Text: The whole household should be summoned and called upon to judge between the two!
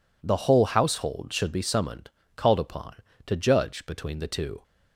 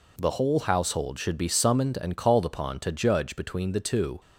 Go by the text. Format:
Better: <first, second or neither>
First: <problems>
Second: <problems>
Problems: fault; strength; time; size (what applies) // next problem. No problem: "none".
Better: second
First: skips "and"; at 2.2 s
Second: none